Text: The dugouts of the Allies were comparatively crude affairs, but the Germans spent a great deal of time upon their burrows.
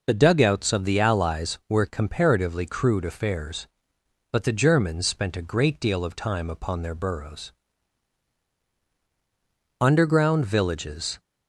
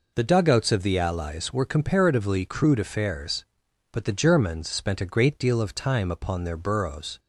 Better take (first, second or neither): second